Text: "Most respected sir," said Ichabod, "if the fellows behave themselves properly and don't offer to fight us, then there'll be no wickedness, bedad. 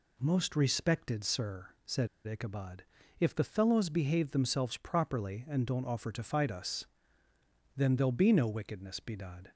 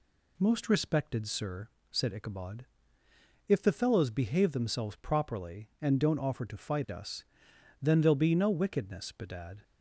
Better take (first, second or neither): second